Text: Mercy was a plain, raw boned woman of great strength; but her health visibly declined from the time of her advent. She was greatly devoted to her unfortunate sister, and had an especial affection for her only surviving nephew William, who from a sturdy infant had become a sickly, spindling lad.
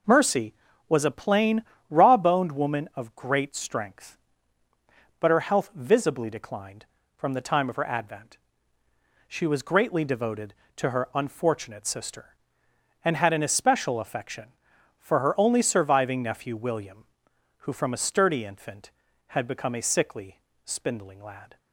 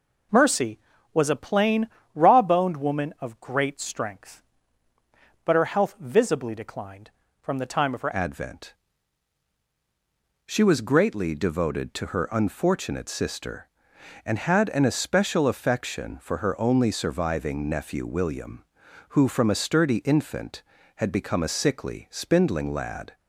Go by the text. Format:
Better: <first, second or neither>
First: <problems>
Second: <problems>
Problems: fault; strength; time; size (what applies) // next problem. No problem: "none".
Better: first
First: none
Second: changes voice at "advent"; from 8.1 s on; 15.0 s long